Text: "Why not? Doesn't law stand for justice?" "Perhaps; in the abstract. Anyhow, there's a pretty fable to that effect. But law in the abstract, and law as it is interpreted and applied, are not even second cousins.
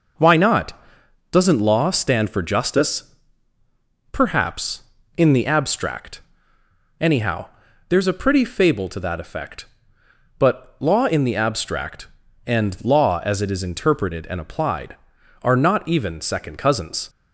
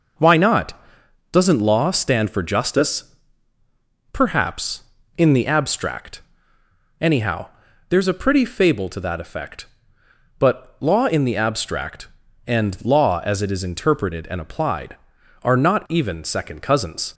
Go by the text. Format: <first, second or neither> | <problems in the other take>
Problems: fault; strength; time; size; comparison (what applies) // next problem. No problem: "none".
neither | none